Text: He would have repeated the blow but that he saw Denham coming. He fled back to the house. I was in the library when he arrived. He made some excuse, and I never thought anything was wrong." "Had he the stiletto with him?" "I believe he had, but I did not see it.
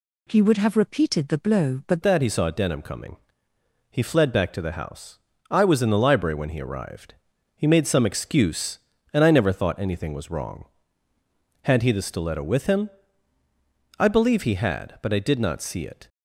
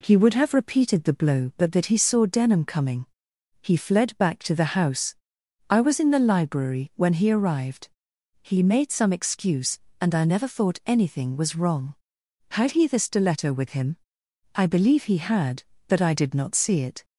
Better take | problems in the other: second | changes voice at "that"; from 2.0 s on; 14.0 s long

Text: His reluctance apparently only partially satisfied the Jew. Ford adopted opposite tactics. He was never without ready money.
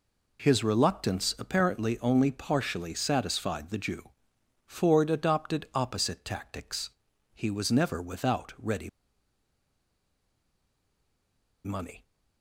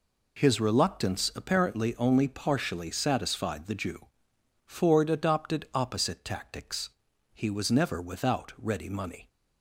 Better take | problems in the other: second | pauses between "ready" and "money"; strong; at 8.8 s; 2.7 s long

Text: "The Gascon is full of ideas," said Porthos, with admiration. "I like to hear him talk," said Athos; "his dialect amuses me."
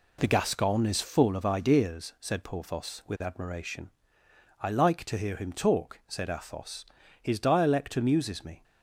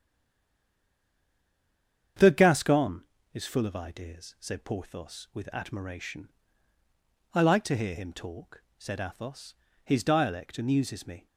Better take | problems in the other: first | stays silent before the first word; until 2.1 s; 2.1 s long // starts louder than the rest; strong; until 3.4 s; 8 dB

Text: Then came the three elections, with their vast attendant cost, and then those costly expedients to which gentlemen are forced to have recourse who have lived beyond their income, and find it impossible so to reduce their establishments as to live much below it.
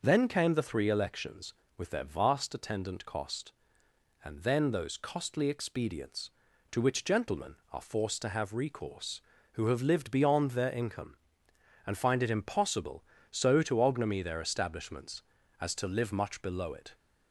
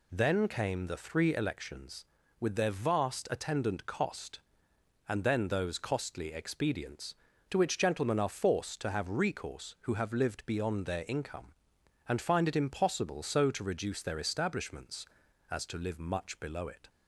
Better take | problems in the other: second | says "ognomy" for "reduce"; at 13.8 s

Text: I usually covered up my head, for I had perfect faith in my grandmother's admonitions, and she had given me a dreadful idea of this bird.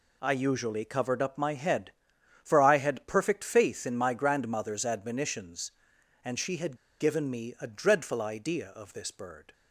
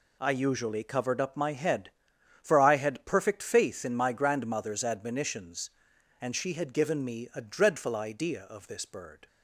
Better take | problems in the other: second | pauses between "had" and "given"; slight; at 6.7 s; 0.22 s long

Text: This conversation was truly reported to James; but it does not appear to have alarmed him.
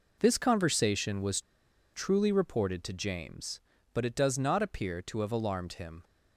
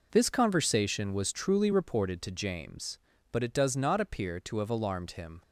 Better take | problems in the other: second | pauses between "was" and "truly"; noticeable; at 1.3 s; 0.53 s long

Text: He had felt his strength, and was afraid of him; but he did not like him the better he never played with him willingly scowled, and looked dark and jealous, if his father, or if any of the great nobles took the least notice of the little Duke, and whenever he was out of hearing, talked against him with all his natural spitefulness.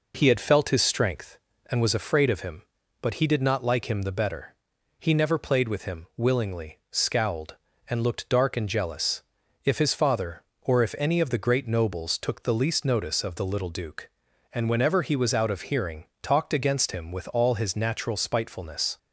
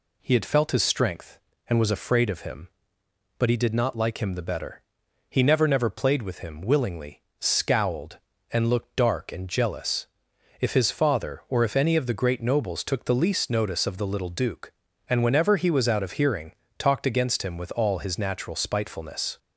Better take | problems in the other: first | pauses between "better" and "he"; noticeable; at 4.8 s; 0.50 s long; also in the first // says "never" twice; at 5.6 s // pauses between "willingly" and "scowled"; slight; at 7.2 s; 0.16 s long

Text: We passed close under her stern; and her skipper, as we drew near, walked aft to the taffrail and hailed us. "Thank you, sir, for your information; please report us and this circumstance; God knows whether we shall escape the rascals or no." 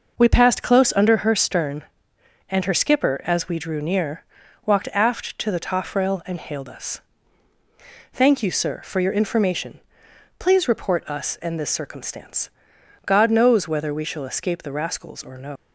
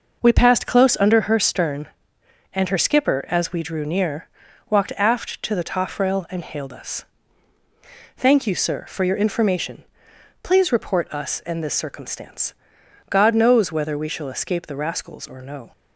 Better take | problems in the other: second | leaves "no" unfinished; at 15.5 s; 120 ms

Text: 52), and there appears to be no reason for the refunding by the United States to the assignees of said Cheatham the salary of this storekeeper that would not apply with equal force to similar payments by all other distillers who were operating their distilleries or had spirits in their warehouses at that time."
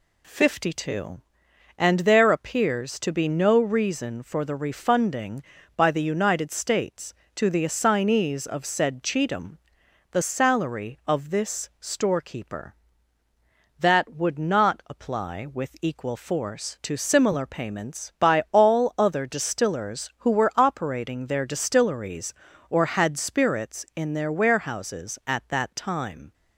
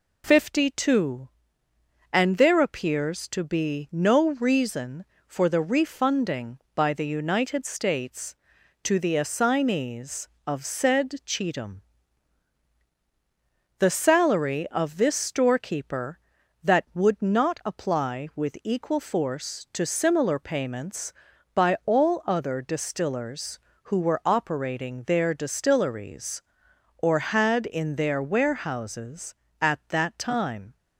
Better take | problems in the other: first | pauses between "Cheatham" and "the"; strong; at 11.8 s; 1.9 s long; noticeable in the first // skips "spirits"; at 27.6 s

